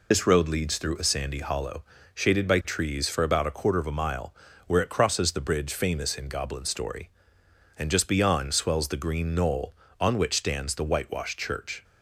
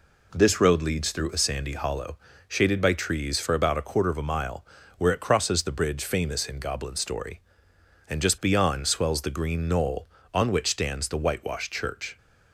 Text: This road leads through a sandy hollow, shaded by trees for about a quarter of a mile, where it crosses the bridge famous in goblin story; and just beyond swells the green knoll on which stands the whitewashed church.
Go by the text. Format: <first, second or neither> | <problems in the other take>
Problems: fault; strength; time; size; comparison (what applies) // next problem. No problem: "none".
second | loses the start of "This"; at 0.1 s; 120 ms